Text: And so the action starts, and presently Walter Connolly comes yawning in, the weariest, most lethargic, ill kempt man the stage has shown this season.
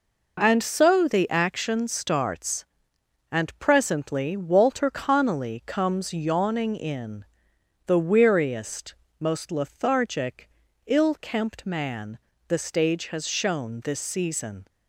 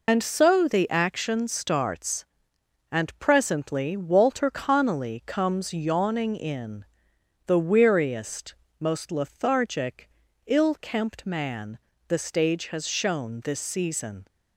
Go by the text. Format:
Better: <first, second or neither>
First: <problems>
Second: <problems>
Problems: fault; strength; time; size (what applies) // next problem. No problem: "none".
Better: first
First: pauses between "man" and "the"; slight; at 12.1 s; 0.28 s long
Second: loses the start of "And"; at 0.0 s; 105 ms // pauses between "man" and "the"; slight; at 11.7 s; 0.28 s long